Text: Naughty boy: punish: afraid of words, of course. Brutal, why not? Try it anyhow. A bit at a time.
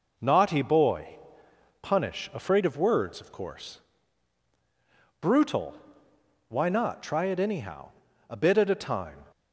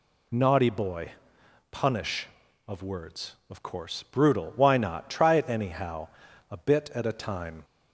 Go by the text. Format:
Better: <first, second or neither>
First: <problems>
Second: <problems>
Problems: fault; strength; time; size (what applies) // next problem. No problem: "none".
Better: first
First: none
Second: skips "afraid"; at 2.4 s